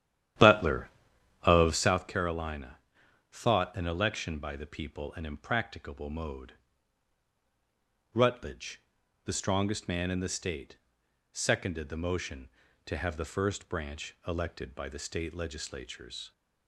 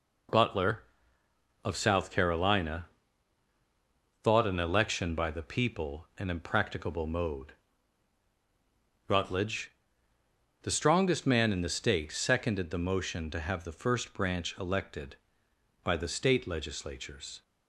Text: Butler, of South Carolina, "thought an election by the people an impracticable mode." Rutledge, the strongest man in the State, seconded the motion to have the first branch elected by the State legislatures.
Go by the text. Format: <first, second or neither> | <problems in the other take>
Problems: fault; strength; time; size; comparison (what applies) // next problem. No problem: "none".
second | starts louder than the rest; strong; until 2.1 s; 11.5 dB